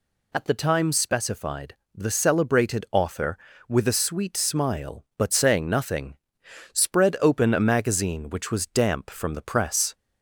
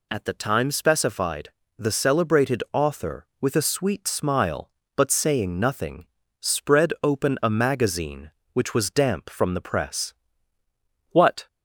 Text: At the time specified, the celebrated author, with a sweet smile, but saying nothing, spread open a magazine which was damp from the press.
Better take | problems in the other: first | goes on to say "What"; slight; from 11.1 s on; 0.36 s long

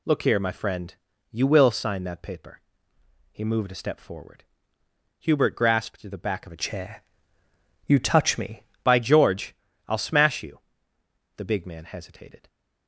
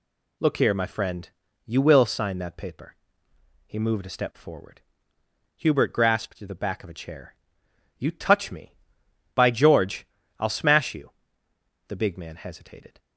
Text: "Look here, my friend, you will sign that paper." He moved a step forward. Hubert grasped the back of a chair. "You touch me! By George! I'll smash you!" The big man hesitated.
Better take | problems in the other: second | changes voice from "chair" to "me"; from 6.5 to 8.6 s; 2.1 s long

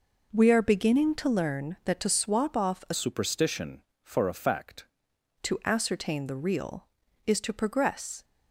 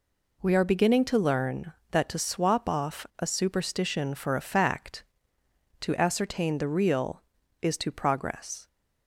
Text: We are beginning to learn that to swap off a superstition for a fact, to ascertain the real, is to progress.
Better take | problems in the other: second | changes voice from "superstition" to "fact"; from 2.9 to 4.8 s; 1.9 s long

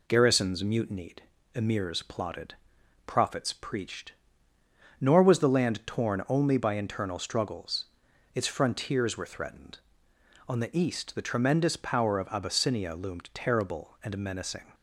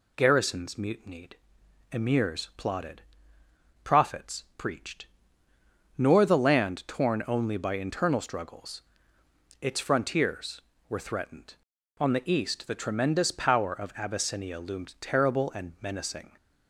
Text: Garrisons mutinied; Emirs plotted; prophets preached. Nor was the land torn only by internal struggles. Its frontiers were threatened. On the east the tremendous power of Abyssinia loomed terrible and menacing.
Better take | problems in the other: first | skips "was"; at 6.2 s

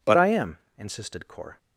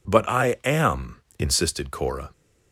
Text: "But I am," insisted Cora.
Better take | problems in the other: second | changes voice at "I"; from 0.1 s on; 1.4 s long

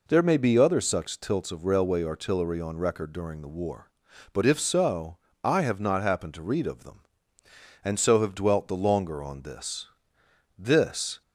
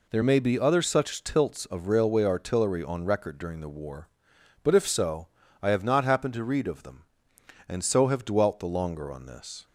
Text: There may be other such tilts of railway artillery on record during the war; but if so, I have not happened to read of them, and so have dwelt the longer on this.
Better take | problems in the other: second | goes on to say "This"; noticeable; from 10.5 s on; 0.62 s long

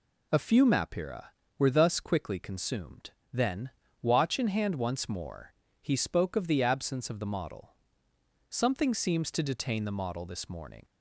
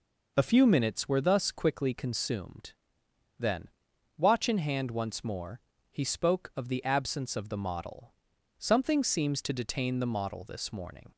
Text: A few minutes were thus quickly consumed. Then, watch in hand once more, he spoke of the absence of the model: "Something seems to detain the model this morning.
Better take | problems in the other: second | says "mapira" for "minutes"; at 0.6 s

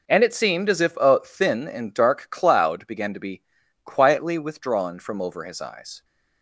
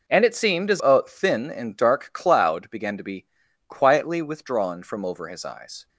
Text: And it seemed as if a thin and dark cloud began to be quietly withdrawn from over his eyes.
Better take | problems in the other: first | skips "if"; at 0.8 s // pauses between "be" and "quietly"; at 3.2 s; 0.42 s long; also in the first

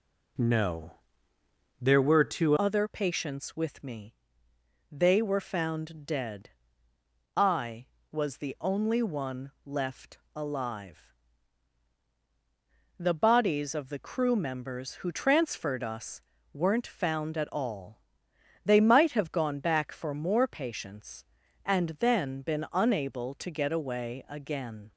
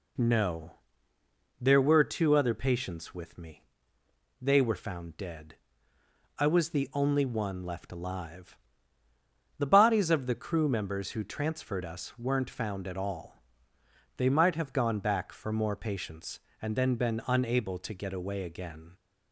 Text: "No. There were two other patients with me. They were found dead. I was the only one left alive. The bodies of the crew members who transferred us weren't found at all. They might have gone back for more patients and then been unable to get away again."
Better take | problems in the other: second | changes voice at "other"; from 2.5 s on; 22.4 s long // pauses between "left" and "alive"; slight; at 10.1 s; 0.18 s long // pauses between "us" and "weren't"; slight; at 16.2 s; 0.30 s long

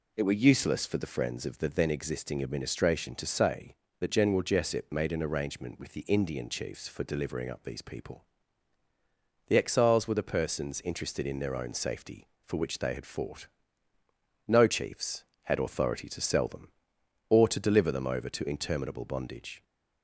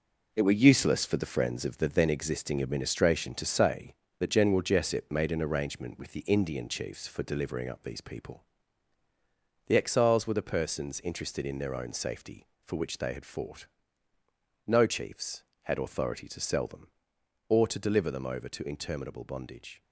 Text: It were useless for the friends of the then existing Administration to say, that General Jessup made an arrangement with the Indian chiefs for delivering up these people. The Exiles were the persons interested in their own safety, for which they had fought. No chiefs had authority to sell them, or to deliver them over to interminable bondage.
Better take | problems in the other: first | gets quieter; strong; throughout; 7.5 dB

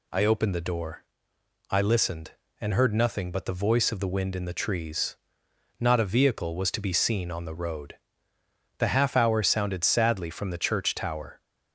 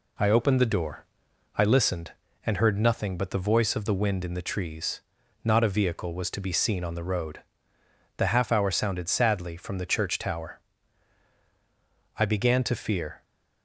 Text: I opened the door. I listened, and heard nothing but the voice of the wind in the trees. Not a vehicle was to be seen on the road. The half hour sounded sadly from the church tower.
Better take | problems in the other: first | goes on to say "I began to fear"; noticeable; from 12.1 s on; 1.0 s long

